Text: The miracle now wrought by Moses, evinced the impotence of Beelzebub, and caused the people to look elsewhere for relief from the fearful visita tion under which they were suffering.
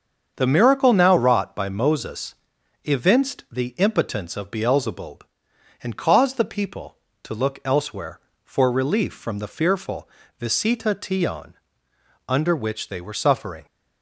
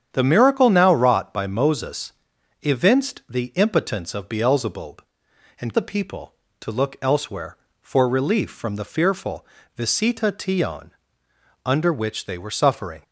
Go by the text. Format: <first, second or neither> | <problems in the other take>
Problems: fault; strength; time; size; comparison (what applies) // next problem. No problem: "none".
first | starts louder than the rest; strong; until 1.1 s; 8.5 dB; also in the first // skips "caused"; at 5.7 s // pauses between "fearful" and "visita"; slight; at 9.4 s; 0.32 s long; slight in the first // pauses between "tion" and "under"; noticeable; at 10.9 s; 0.74 s long; noticeable in the first